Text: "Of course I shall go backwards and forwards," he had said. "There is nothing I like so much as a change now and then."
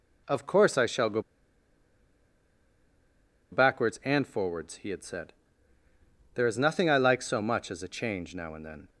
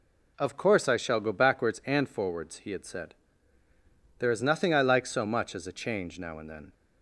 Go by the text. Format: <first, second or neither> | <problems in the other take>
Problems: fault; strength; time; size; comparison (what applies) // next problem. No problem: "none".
second | pauses between "go" and "backwards"; strong; at 1.1 s; 2.3 s long